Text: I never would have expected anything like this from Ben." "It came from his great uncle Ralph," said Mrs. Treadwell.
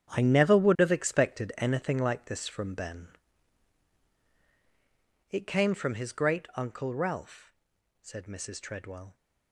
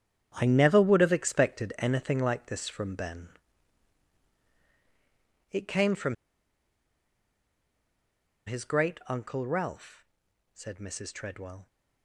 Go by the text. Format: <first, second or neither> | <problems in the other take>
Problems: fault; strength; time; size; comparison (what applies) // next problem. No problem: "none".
first | starts louder than the rest; strong; until 1.3 s; 8.5 dB; strong in the first // pauses between "from" and "his"; strong; at 6.1 s; 2.3 s long